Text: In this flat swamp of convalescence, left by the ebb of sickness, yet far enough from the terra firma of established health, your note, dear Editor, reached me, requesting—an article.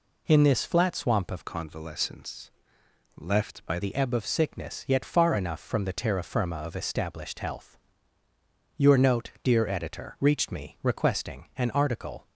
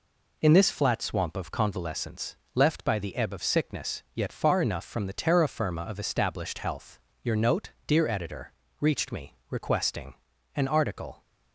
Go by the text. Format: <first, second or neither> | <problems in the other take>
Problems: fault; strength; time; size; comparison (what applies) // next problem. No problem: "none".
second | changes voice from "convalescence" to "by"; from 1.4 to 3.7 s; 2.3 s long